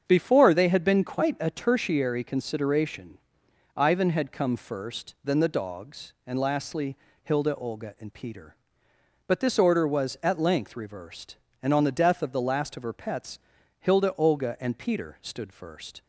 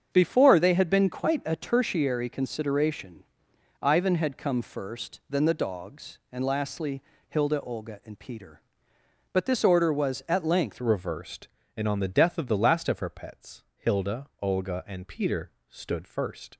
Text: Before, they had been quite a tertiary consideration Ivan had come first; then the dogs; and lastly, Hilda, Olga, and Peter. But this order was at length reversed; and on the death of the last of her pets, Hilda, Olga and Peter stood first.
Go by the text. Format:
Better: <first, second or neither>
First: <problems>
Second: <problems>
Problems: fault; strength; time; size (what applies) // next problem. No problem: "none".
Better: first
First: starts louder than the rest; strong; until 1.0 s; 7.5 dB // pauses between "consideration" and "Ivan"; noticeable; at 3.1 s; 0.58 s long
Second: starts louder than the rest; strong; until 1.1 s; 7.5 dB // pauses between "consideration" and "Ivan"; noticeable; at 3.2 s; 0.58 s long // changes voice at "reversed"; from 10.8 s on; 5.7 s long // pauses between "Peter" and "stood"; slight; at 15.5 s; 0.18 s long